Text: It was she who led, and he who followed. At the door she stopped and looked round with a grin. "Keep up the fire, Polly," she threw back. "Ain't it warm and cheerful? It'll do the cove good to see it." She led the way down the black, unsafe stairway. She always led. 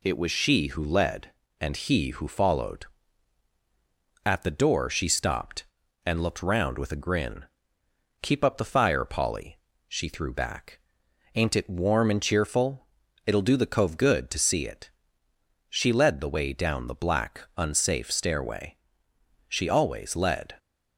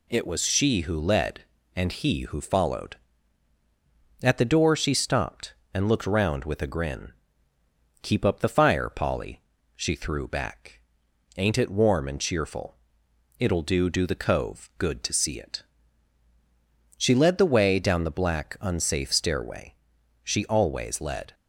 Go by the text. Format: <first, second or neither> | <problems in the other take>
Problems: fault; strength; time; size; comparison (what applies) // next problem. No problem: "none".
first | says "do" twice; at 13.8 s